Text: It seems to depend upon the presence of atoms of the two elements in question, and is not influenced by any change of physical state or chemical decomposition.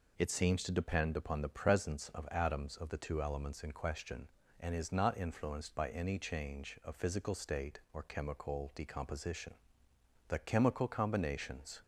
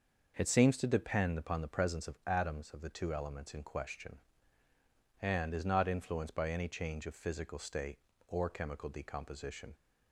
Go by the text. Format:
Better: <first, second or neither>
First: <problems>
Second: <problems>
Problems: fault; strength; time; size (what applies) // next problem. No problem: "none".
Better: second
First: goes on to say "The chemical combinations"; from 10.2 s on; 1.5 s long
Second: none